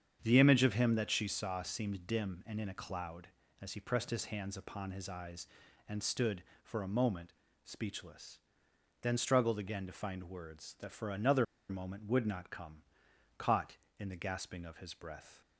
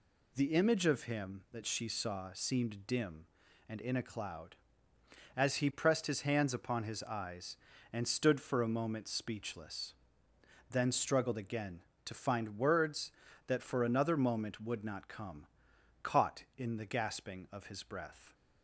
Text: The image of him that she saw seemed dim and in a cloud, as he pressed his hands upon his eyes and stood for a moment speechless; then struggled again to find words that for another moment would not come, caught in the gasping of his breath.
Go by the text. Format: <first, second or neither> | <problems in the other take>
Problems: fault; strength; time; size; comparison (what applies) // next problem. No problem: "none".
second | starts louder than the rest; strong; until 1.2 s; 8 dB // pauses between "moment" and "speechless"; slight; at 7.3 s; 0.32 s long // pauses between "another" and "moment"; slight; at 11.4 s; 0.25 s long